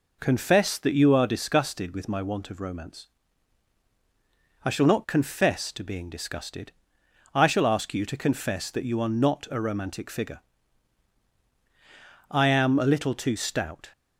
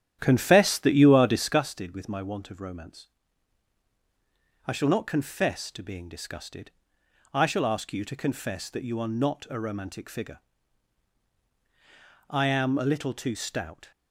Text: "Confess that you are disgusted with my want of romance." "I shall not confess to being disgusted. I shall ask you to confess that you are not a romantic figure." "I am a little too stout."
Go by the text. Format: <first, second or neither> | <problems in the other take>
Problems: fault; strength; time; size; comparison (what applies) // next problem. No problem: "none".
first | starts louder than the rest; strong; until 1.6 s; 10.5 dB